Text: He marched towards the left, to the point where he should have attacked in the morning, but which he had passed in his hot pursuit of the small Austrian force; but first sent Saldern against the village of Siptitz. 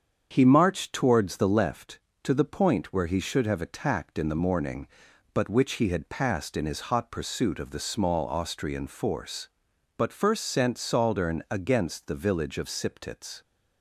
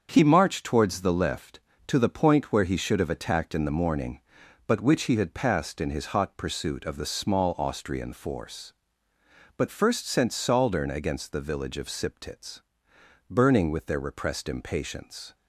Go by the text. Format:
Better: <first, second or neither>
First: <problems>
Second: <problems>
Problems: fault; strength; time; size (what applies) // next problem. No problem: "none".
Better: first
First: starts louder than the rest; strong; until 1.3 s; 7.5 dB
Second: starts louder than the rest; strong; until 1.1 s; 7 dB // goes on to say "Burning with their repressed impatience"; strong; from 13.2 s on; 2.0 s long